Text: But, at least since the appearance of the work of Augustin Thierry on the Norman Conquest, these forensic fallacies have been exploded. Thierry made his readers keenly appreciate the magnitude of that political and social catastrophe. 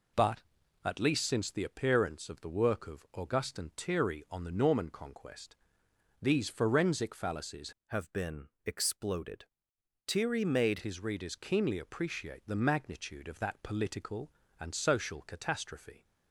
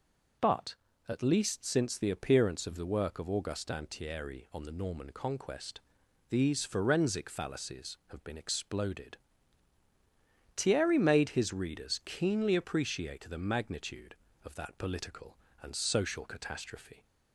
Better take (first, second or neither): second